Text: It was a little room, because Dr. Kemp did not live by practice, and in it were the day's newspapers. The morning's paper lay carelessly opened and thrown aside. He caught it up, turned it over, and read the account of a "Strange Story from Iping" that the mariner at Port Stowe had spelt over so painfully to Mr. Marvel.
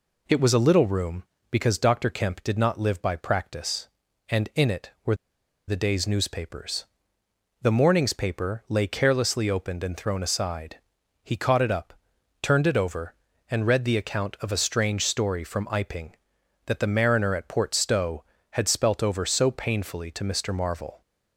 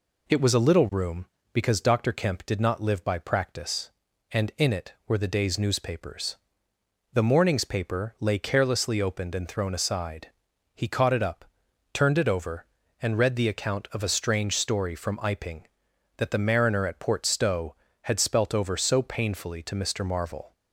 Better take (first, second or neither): second